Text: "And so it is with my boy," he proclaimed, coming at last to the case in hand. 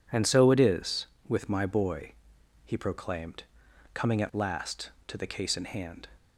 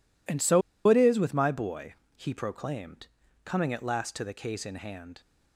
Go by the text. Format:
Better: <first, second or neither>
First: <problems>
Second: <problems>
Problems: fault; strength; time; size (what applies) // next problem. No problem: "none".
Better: first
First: none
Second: pauses between "so" and "it"; slight; at 0.6 s; 0.27 s long